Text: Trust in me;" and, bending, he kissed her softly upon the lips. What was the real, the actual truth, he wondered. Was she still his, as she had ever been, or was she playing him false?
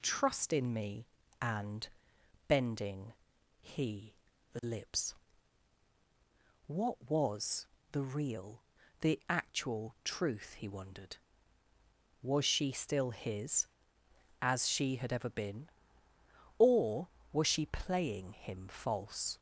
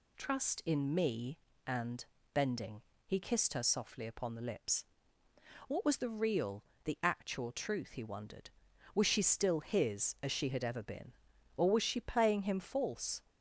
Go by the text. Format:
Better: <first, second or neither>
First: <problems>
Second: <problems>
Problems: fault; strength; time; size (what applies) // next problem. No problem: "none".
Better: second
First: skips "kissed her softly upon"; at 4.3 s // pauses between "was" and "the"; slight; at 7.6 s; 0.28 s long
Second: none